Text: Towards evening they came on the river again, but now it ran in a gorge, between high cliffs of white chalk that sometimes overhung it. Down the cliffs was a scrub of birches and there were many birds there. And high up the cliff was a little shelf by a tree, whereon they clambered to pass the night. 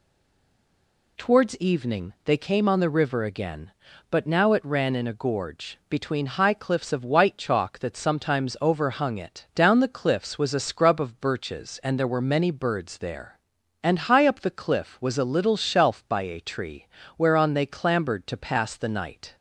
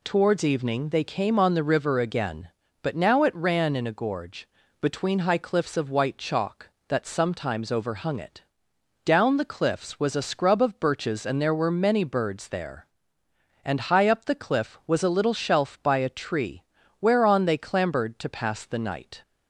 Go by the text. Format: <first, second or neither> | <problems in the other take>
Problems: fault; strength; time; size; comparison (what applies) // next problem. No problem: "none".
second | stays silent before the first word; until 1.1 s; 1.1 s long